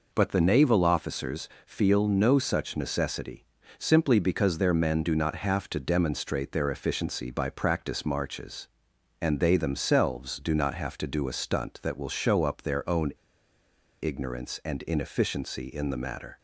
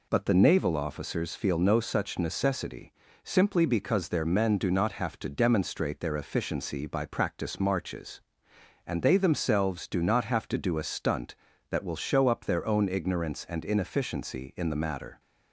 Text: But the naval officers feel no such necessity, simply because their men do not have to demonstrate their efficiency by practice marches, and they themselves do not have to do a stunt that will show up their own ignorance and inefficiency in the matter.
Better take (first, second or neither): second